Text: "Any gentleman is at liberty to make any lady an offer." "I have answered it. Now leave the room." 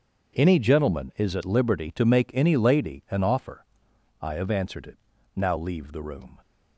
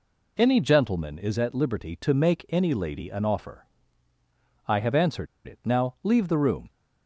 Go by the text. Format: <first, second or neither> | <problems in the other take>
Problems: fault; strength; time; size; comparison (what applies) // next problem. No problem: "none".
first | pauses between "answered" and "it"; slight; at 5.2 s; 0.19 s long